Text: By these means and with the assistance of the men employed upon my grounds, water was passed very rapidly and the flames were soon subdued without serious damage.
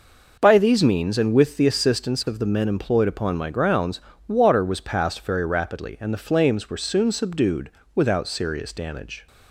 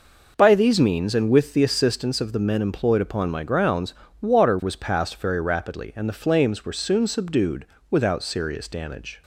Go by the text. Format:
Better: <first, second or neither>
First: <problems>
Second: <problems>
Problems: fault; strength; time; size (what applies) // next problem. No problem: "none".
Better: neither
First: pauses between "subdued" and "without"; slight; at 7.6 s; 0.26 s long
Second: pauses between "subdued" and "without"; slight; at 7.6 s; 0.26 s long